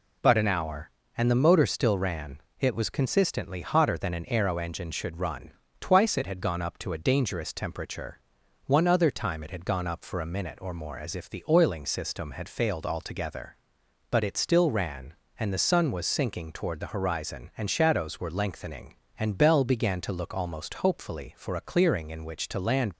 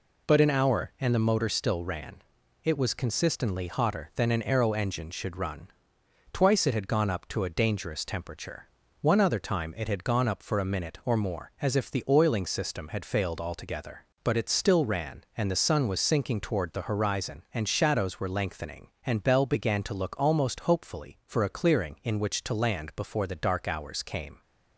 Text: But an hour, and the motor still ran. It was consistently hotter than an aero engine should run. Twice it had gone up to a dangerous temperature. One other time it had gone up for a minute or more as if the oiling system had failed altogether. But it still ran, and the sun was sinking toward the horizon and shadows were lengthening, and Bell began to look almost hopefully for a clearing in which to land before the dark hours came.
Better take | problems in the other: second | stops before "before the dark hours came"; at 22.9 s

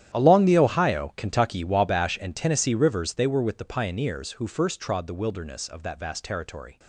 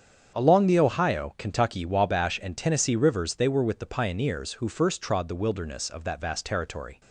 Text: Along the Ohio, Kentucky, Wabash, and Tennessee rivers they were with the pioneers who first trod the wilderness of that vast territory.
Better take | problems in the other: second | gets quieter; strong; throughout; 17.5 dB // starts louder than the rest; strong; until 1.2 s; 11 dB; strong in the second

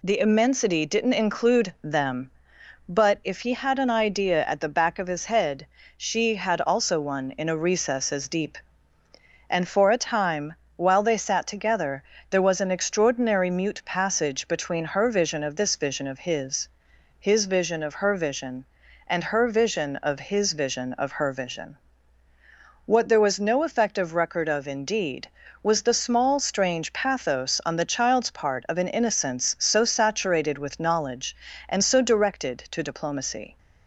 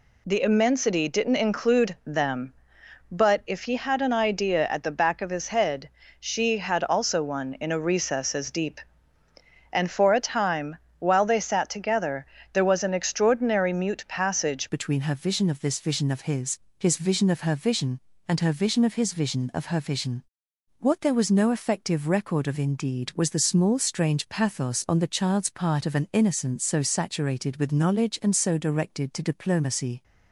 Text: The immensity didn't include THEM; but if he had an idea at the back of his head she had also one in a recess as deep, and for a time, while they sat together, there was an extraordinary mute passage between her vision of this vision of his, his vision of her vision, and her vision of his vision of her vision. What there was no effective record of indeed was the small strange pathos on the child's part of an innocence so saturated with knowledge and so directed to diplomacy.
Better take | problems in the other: first | pauses between "head" and "she"; slight; at 5.8 s; 0.28 s long; slight in the first // changes voice at "between"; from 14.6 s on; 15.4 s long

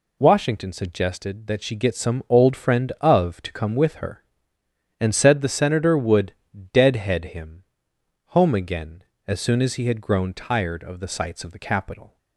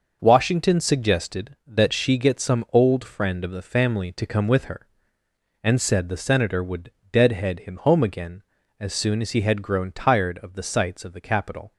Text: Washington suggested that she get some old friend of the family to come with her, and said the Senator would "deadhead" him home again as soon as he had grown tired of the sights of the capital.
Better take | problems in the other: second | skips "the family"; at 3.4 s // pauses between "would" and "deadhead"; at 6.3 s; 0.40 s long; slight in the second // pauses between "him" and "home"; noticeable; at 7.6 s; 0.70 s long

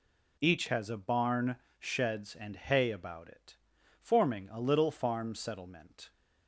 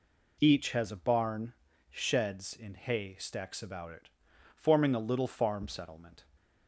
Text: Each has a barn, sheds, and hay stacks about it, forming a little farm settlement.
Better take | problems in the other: second | skips "stacks"; at 2.9 s

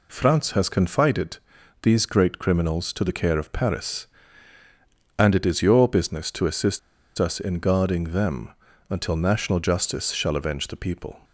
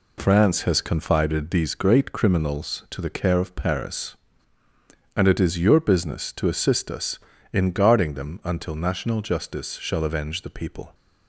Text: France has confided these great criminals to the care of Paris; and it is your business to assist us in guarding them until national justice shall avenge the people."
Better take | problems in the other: second | pauses between "confided" and "these"; noticeable; at 1.3 s; 0.46 s long // pauses between "assist" and "us"; at 6.7 s; 0.39 s long // pauses between "them" and "until"; at 8.5 s; 0.38 s long

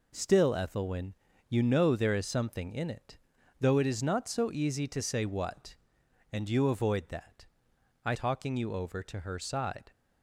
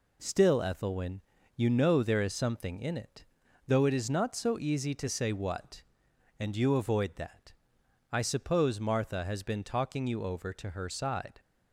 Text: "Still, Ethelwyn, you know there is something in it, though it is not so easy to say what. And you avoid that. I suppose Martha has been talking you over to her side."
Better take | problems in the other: second | skips "suppose Martha has been"; at 8.1 s

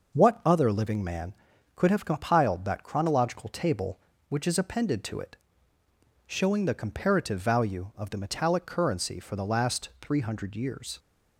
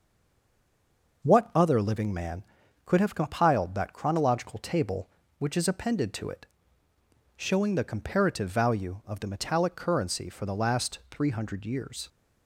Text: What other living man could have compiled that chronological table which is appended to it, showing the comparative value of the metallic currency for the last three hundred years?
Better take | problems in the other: first | stays silent before the first word; noticeable; until 1.2 s; 1.2 s long

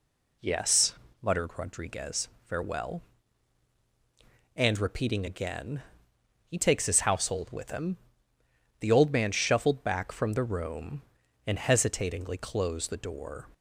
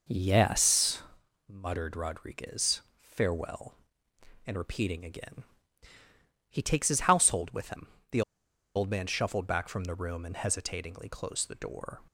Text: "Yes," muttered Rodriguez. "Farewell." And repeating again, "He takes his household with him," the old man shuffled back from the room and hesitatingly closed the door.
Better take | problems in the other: first | pauses between "the" and "old"; noticeable; at 8.2 s; 0.54 s long

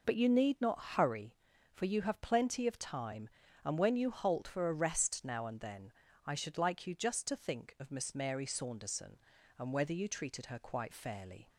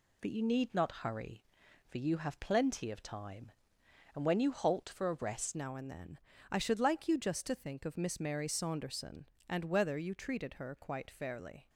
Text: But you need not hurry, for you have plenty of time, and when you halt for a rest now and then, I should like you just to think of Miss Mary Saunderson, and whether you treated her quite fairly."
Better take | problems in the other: first | changes voice at "now"; from 5.5 s on; 6.1 s long

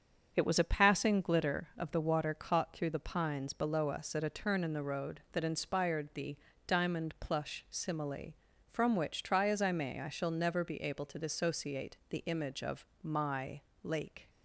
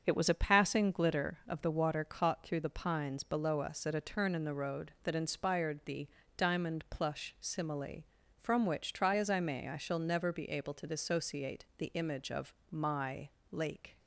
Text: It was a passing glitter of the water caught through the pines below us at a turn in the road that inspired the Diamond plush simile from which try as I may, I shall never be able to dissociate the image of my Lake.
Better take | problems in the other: neither | starts louder than the rest; the same in both // pauses between "the" and "Diamond"; slight; the same in both // pauses between "of" and "my"; slight; the same in both // pauses between "my" and "Lake"; slight; the same in both

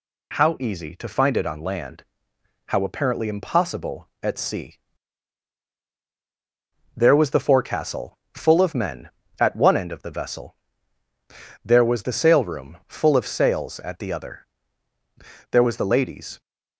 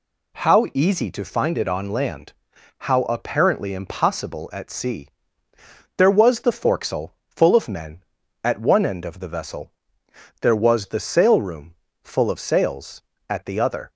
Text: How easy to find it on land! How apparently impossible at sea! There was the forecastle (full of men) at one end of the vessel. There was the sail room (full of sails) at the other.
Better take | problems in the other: second | goes on to say "There was the ladies"; noticeable; from 15.4 s on; 0.90 s long

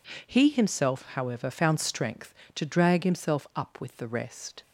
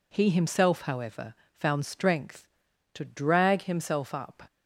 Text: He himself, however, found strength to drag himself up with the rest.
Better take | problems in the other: first | stops before "with the rest"; at 4.4 s

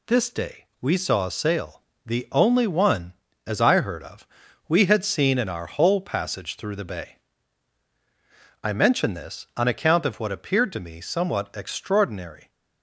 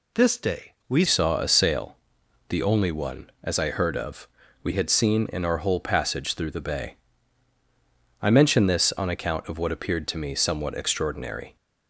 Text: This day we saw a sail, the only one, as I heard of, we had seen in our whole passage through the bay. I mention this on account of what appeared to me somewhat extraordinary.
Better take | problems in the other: first | changes voice at "saw"; from 1.0 s on; 10.5 s long

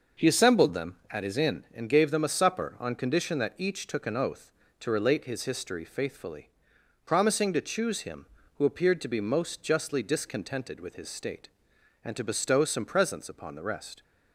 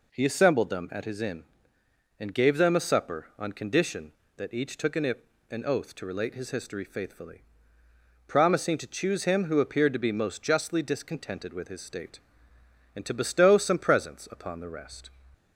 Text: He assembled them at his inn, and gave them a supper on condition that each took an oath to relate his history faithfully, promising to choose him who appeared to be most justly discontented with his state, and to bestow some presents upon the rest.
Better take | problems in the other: first | says "an" twice; at 5.5 s

